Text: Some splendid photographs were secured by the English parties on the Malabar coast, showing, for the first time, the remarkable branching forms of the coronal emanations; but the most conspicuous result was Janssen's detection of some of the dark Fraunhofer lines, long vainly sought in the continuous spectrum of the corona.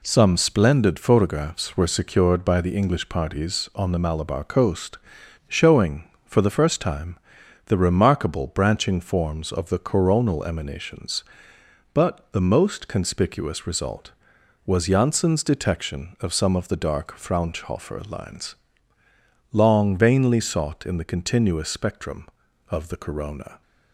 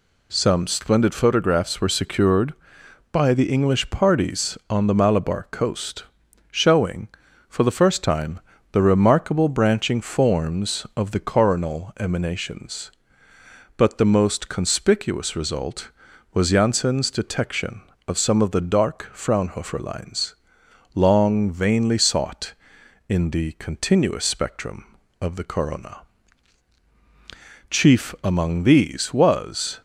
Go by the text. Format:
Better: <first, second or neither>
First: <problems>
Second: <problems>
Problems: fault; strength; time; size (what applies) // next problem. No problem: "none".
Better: first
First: none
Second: goes on to say "Chief among these was"; strong; from 27.7 s on; 2.0 s long